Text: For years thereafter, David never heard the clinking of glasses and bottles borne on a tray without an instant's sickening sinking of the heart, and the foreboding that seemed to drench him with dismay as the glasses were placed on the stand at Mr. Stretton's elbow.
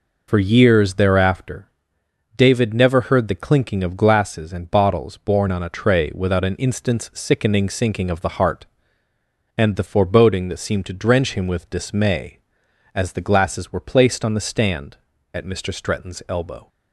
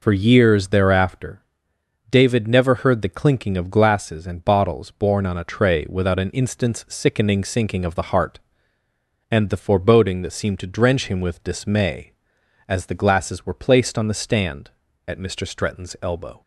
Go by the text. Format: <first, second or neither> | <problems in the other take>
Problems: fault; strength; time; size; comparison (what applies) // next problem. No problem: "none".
neither | none